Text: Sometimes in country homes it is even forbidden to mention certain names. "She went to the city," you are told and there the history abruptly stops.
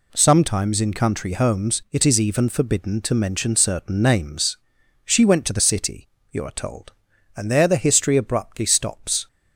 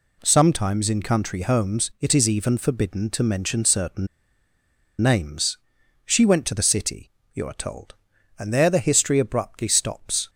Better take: first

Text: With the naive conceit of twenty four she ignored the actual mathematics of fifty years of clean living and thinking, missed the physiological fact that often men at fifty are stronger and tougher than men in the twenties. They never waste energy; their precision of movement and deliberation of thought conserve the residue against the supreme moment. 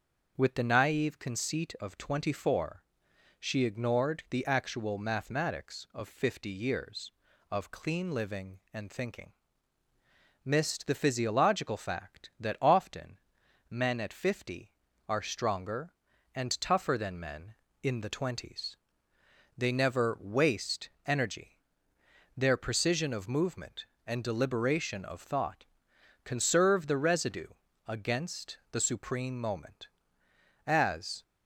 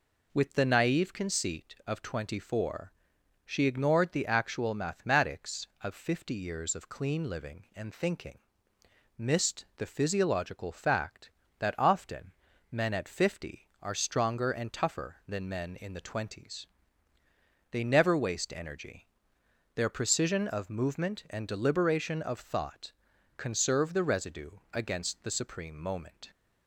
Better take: second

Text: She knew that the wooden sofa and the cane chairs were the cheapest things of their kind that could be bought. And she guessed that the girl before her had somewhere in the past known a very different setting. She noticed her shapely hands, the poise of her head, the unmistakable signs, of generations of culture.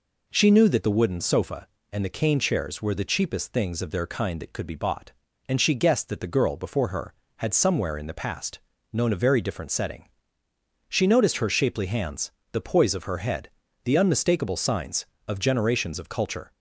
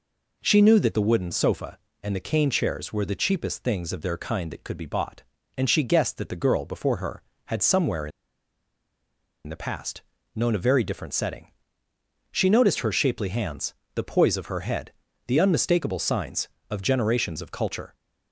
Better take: first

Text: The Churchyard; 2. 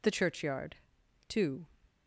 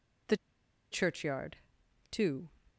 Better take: first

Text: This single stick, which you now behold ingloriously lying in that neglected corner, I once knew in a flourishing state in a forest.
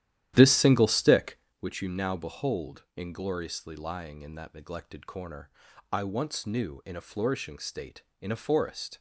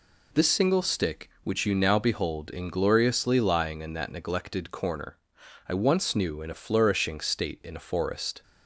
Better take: second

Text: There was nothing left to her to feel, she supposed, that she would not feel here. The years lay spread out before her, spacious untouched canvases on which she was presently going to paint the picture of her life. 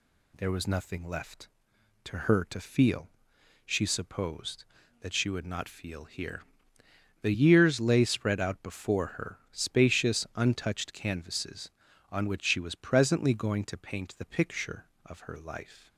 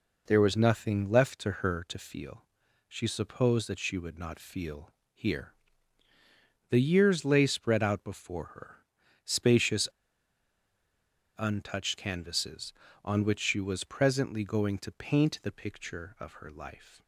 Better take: first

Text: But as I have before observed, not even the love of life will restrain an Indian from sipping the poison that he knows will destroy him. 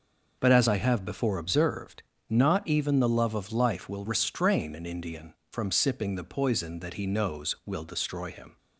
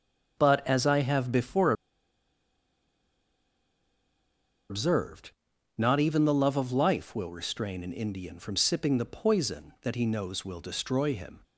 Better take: first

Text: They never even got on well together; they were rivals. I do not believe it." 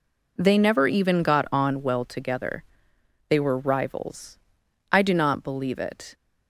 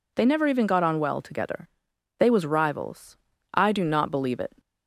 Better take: first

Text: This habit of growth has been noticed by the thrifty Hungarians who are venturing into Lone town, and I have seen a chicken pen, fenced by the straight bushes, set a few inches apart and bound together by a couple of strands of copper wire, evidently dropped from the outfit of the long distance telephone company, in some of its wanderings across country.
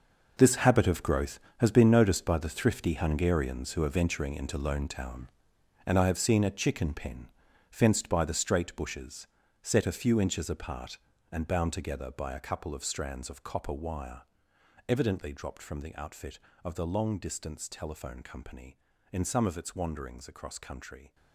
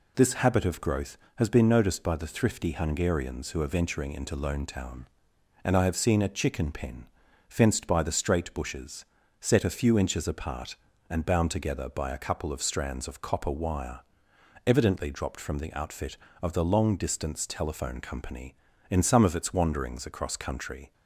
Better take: second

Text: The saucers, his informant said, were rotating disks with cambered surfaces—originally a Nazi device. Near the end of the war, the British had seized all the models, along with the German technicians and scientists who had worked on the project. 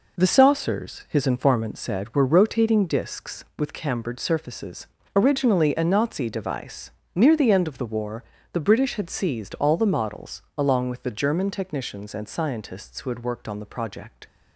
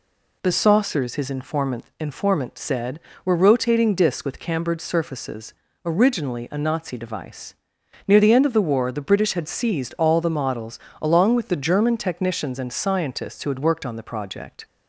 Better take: first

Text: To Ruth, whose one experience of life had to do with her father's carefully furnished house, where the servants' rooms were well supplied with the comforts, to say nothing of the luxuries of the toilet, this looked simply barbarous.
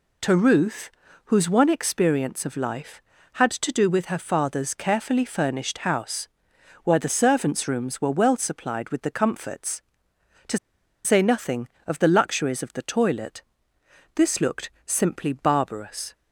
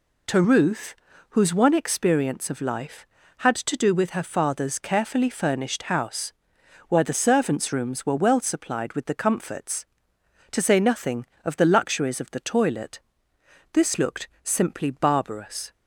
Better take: second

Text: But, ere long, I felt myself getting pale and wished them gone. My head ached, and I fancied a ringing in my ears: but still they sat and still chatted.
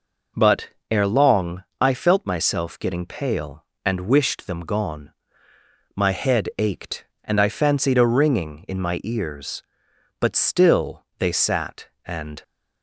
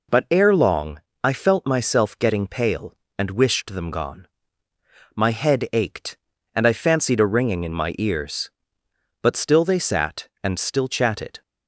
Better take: second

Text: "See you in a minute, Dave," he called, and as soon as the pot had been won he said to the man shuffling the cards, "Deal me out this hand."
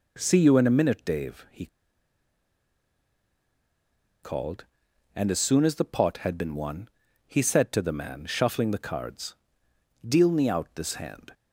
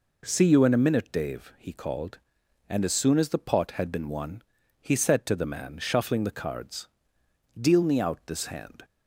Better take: second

